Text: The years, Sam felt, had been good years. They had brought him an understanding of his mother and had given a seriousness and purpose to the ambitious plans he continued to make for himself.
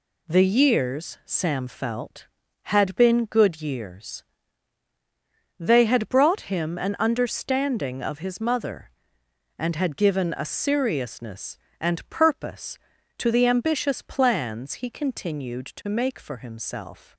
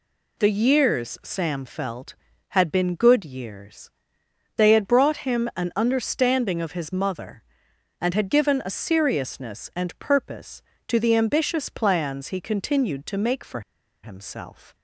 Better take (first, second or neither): first